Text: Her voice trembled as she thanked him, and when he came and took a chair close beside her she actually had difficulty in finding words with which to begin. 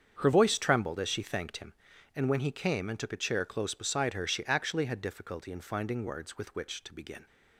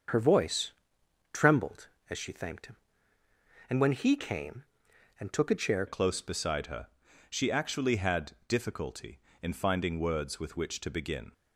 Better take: first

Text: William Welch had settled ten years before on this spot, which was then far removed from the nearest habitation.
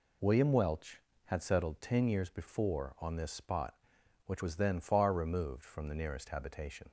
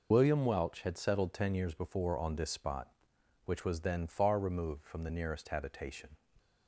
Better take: first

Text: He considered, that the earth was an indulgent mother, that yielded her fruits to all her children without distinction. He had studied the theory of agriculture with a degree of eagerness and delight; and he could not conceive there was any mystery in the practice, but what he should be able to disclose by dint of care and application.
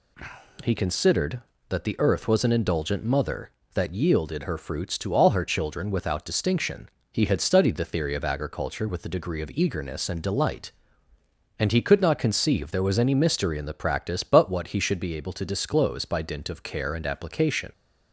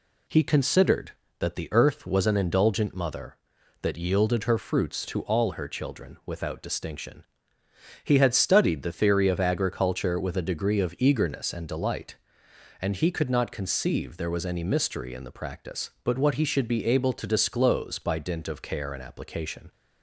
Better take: neither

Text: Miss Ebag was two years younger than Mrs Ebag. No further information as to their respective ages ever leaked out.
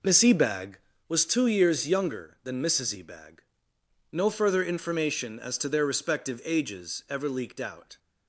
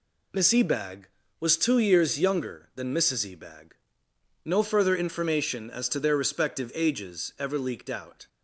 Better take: second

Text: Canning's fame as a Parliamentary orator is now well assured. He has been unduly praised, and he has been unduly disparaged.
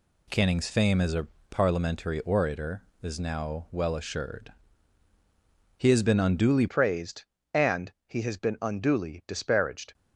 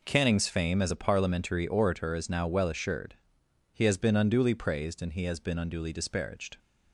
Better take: second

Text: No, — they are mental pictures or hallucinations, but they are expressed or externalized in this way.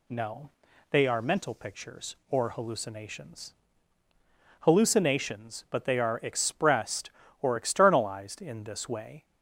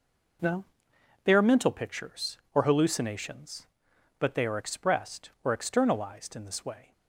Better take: second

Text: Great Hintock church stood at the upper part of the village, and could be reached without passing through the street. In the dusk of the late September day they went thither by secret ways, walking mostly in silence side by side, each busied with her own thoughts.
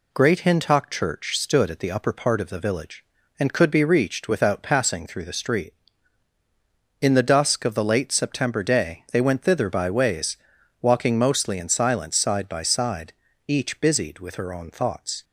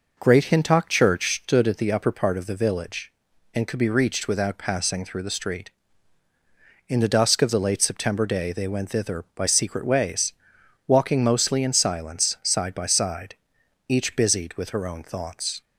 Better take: second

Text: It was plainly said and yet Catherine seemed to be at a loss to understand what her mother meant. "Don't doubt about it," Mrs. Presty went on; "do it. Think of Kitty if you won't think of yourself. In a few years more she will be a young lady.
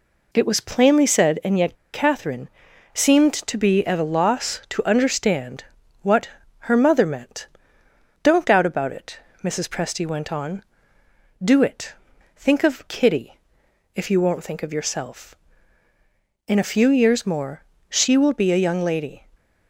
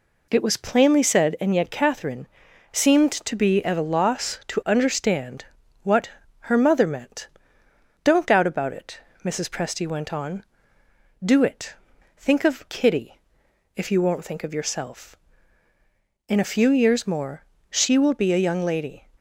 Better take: second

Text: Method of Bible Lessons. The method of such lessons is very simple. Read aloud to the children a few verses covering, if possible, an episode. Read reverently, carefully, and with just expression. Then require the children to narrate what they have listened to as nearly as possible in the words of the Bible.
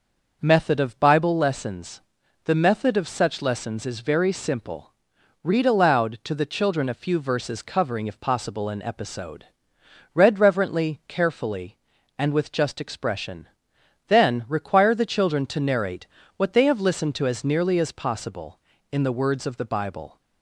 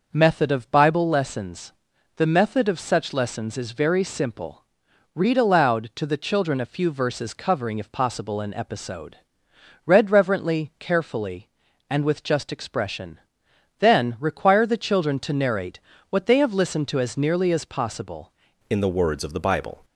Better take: first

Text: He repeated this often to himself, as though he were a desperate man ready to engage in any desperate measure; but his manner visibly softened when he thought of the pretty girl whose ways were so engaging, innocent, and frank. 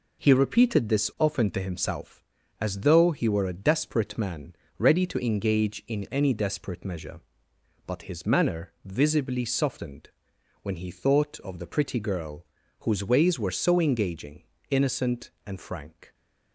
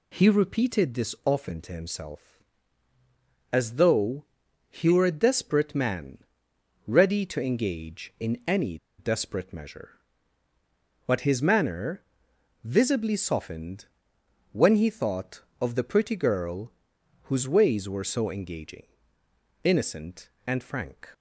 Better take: first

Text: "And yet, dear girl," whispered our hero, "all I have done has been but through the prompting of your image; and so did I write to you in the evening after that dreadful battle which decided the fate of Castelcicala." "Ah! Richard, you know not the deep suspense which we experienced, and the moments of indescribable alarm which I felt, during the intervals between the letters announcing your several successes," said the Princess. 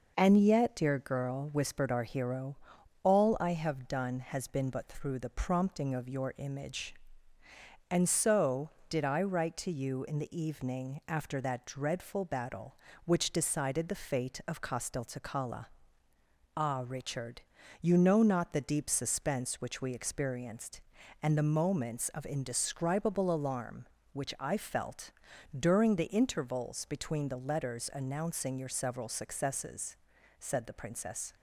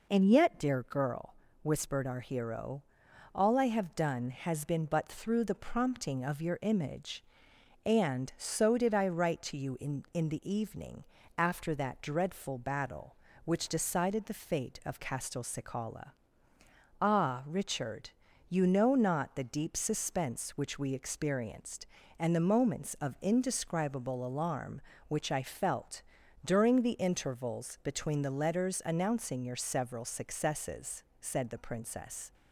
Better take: first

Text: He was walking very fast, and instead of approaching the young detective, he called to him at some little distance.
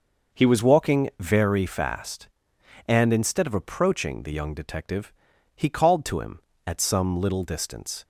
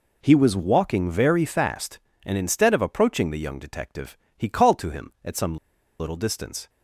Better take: first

